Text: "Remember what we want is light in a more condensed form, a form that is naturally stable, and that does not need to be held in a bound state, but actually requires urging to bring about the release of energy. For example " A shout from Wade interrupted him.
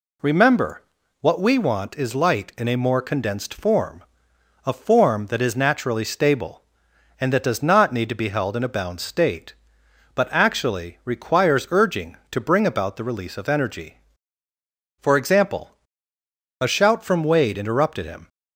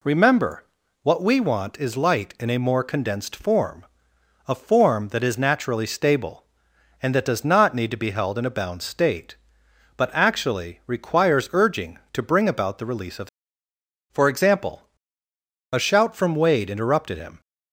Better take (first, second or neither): first